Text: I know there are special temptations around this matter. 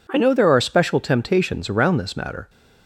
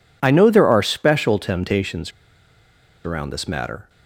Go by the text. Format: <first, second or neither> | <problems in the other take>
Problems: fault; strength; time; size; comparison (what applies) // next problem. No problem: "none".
first | pauses between "temptations" and "around"; noticeable; at 2.1 s; 0.94 s long